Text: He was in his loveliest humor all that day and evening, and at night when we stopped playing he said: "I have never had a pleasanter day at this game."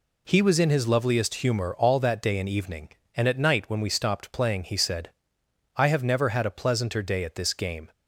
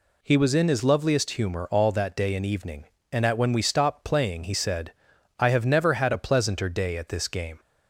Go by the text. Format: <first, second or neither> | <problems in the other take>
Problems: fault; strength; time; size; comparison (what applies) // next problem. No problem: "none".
first | skips "night"; at 3.3 s